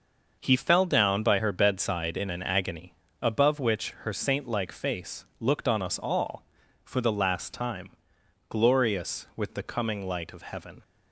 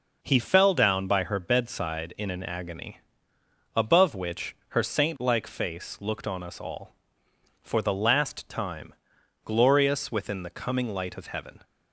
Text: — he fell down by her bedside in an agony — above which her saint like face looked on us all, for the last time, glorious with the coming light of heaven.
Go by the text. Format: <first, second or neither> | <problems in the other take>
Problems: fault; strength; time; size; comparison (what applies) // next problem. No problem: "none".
first | says "within" for "with"; at 10.0 s